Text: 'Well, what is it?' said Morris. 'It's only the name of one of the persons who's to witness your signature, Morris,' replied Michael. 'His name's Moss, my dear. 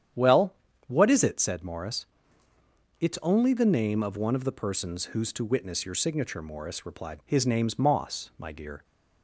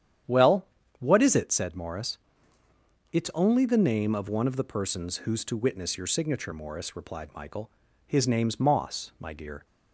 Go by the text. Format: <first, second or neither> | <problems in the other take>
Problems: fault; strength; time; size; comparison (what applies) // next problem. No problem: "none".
second | starts louder than the rest; strong; until 1.5 s; 9.5 dB; strong in the second // skips "Michael"; at 7.2 s